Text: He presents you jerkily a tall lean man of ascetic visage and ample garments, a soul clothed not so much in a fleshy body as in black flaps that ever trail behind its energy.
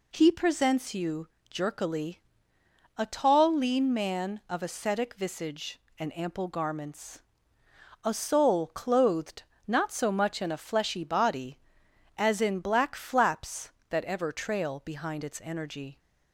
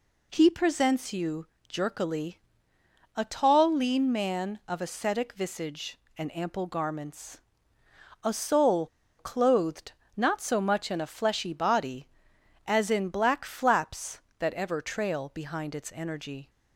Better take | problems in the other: first | pauses between "you" and "jerkily"; slight; at 1.4 s; 0.20 s long; slight in the first // pauses between "jerkily" and "a"; noticeable; at 2.3 s; 0.78 s long; noticeable in the first // pauses between "soul" and "clothed"; slight; at 8.8 s; 0.32 s long // pauses between "clothed" and "not"; slight; at 9.9 s; 0.24 s long; slight in the first

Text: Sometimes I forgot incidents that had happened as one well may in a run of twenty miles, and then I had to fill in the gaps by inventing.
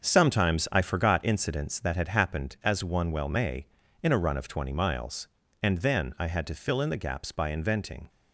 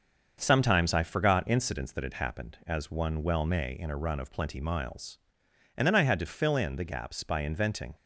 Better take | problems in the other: first | starts louder than the rest; until 1.4 s; 6.5 dB; strong in the first // says "plenty" for "twenty"; at 4.3 s

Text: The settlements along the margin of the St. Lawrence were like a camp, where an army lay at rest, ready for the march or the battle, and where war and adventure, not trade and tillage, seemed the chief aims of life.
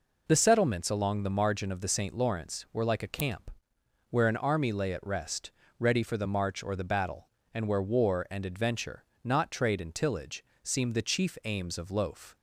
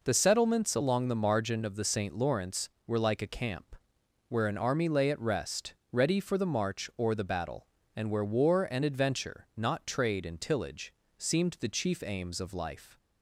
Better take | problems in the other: second | says "loaf" for "life"; at 11.8 s

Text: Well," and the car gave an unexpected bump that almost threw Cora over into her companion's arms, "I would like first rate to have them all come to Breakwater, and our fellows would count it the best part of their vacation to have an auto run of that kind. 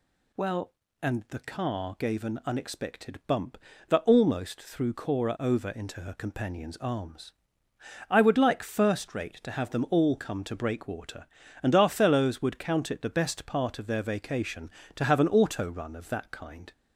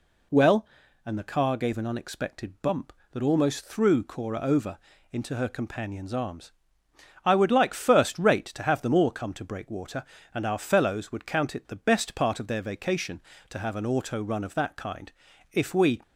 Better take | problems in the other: first | pauses between "over" and "into"; slight; at 4.7 s; 0.34 s long // goes on to say "If we"; slight; from 15.5 s on; 0.48 s long

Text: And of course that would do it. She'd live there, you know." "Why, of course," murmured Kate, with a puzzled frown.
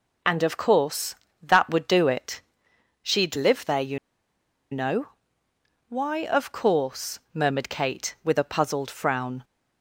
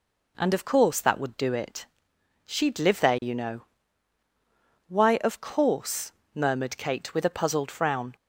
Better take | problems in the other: second | pauses between "you" and "know"; noticeable; at 3.9 s; 0.73 s long

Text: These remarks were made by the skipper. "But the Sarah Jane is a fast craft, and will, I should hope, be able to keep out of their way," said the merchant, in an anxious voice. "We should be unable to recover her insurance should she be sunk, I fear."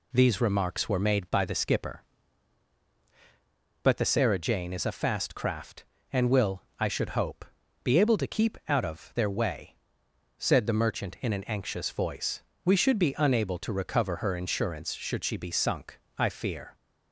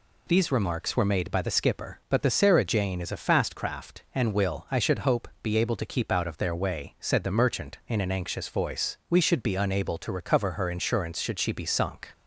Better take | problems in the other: first | stops before "I fear"; at 12.1 s

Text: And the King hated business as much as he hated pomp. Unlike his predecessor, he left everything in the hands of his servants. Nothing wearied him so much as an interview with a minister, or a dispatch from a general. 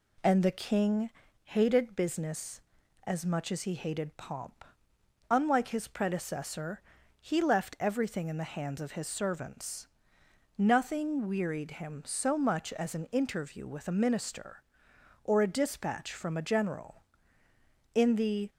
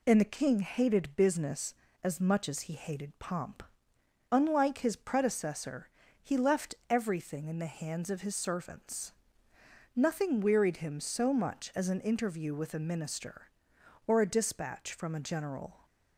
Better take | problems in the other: second | pauses between "King" and "hated"; slight; at 1.0 s; 0.34 s long // goes on to say "In the"; from 17.9 s on; 0.54 s long

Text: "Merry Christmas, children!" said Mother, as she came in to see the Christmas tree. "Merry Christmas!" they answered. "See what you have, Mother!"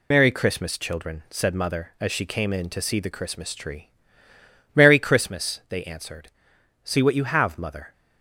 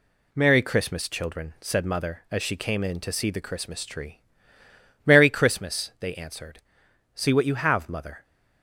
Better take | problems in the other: second | loses the start of "Merry"; at 0.1 s; 80 ms

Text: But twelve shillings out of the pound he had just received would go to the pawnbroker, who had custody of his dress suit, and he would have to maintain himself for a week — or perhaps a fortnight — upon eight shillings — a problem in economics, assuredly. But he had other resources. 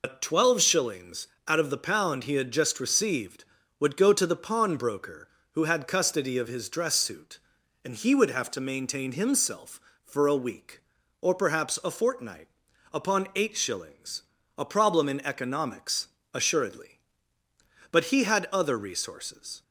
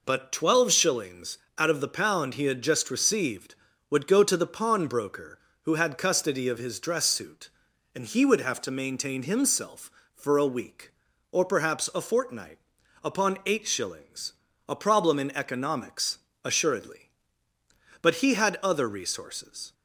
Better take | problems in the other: second | loses the start of "But"; at 0.0 s; 100 ms // pauses between "shillings" and "out"; slight; at 1.2 s; 0.18 s long; slight in the second

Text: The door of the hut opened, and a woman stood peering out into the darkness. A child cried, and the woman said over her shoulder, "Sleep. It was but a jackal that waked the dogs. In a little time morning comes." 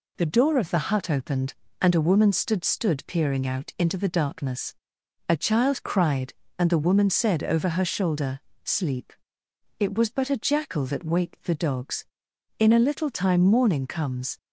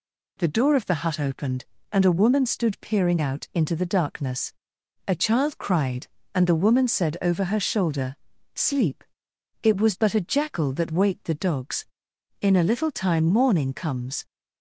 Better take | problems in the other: second | says "stood" twice; at 2.6 s

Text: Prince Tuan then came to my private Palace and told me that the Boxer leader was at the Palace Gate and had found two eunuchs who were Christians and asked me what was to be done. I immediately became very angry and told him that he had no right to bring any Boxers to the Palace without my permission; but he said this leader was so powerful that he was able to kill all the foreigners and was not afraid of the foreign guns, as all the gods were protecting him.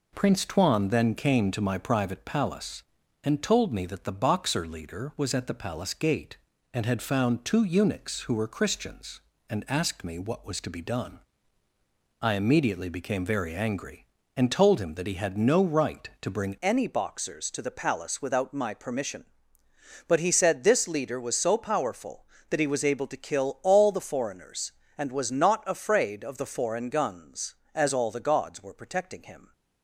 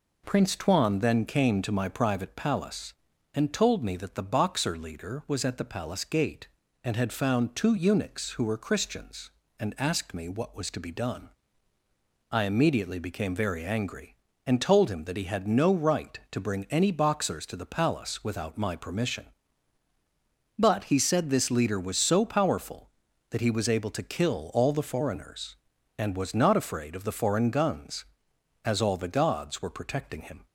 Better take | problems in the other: second | changes voice at "any"; from 16.5 s on; 13.0 s long

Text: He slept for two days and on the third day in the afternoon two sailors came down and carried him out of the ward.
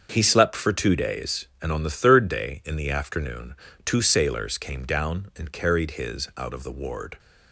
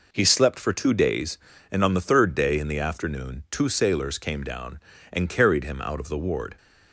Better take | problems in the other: second | starts louder than the rest; until 1.1 s; 6.5 dB // pauses between "afternoon" and "two"; slight; at 3.5 s; 0.30 s long // says "his" for "him"; at 5.9 s

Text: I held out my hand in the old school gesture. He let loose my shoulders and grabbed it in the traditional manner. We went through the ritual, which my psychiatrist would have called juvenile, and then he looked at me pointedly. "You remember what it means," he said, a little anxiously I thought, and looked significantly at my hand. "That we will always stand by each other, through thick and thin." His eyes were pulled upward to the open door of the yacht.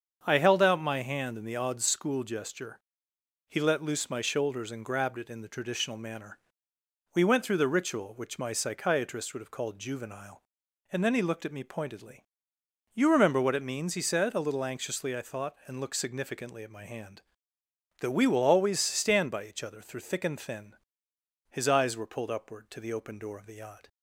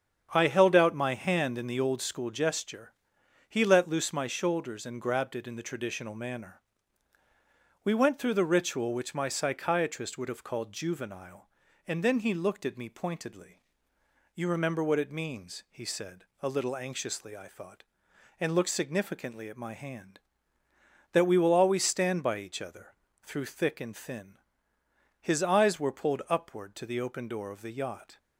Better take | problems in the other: second | starts louder than the rest; strong; until 1.2 s; 7 dB; strong in the second // says "odd" for "old"; at 1.5 s

